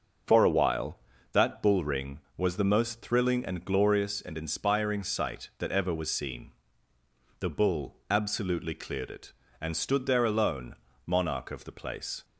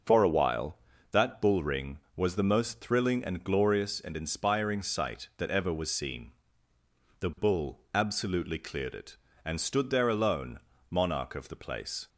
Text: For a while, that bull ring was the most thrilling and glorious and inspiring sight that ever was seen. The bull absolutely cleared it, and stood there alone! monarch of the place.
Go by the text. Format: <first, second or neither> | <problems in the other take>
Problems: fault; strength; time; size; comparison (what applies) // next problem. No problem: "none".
neither | starts louder than the rest; noticeable; the same in both